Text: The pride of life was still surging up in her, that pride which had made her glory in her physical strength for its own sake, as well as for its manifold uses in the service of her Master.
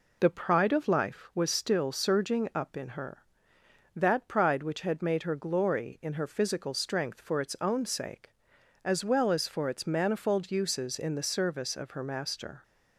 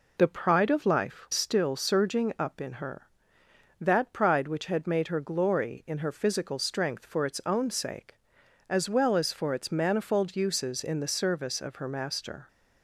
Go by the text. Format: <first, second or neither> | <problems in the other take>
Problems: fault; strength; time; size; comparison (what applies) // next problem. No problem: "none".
first | skips "was"; at 1.3 s